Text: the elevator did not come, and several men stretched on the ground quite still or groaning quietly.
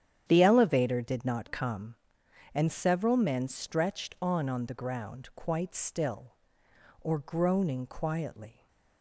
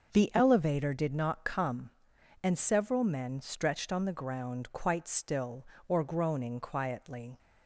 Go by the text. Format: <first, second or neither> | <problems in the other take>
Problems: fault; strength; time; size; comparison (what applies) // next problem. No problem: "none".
second | starts louder than the rest; strong; until 1.2 s; 9.5 dB; also in the second // says "on" twice; at 4.4 s